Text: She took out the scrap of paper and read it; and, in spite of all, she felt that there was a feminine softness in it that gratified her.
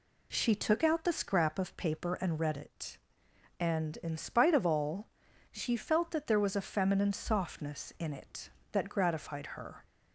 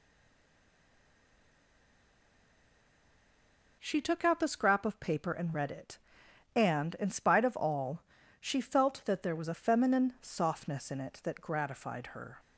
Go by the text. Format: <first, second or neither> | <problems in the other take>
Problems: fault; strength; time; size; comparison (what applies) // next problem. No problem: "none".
first | stays silent before the first word; strong; until 3.7 s; 3.7 s long